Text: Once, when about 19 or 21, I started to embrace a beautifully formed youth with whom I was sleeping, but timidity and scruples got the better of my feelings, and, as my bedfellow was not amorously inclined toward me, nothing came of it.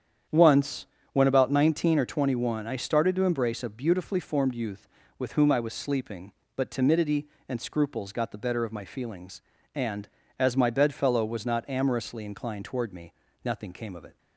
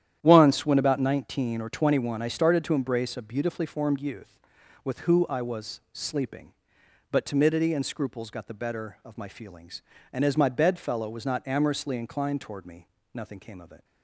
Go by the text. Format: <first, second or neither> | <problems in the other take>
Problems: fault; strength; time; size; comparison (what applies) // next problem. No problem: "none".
first | starts louder than the rest; strong; until 1.2 s; 10.5 dB; strong in the first // says "who" for "whom"; at 5.0 s